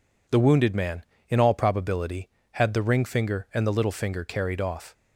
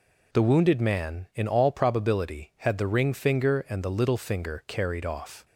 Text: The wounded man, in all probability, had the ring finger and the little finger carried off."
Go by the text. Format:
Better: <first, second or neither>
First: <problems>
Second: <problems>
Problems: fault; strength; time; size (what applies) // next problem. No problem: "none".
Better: neither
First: none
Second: none